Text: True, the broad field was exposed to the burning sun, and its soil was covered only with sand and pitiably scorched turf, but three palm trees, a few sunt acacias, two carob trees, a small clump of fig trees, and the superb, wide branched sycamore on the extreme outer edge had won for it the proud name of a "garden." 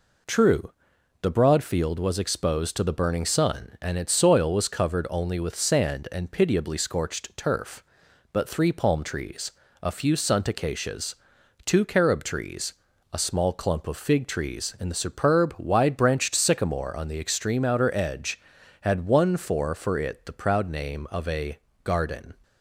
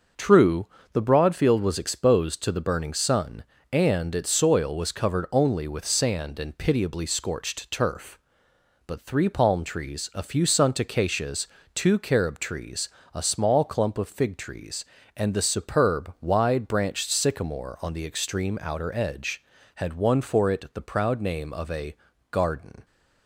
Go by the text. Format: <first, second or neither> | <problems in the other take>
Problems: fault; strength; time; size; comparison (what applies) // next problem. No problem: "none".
second | says "for" twice; at 19.7 s // pauses between "a" and "garden"; slight; at 21.5 s; 0.26 s long; slight in the second